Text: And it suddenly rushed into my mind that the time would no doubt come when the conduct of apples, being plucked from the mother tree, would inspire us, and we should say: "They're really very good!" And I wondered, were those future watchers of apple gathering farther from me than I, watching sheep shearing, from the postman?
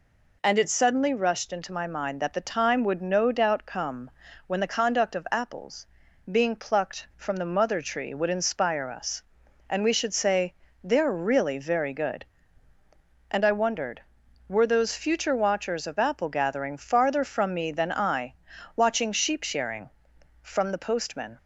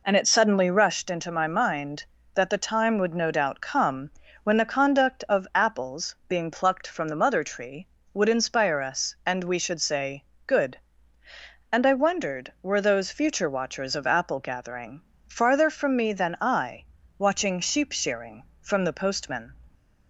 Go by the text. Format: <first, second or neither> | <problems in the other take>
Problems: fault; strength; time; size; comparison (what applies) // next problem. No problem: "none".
first | pauses between "come" and "when"; slight; at 4.1 s; 0.32 s long; also in the first // skips "They're really very"; at 10.3 s // pauses between "gathering" and "farther"; slight; at 15.0 s; 0.24 s long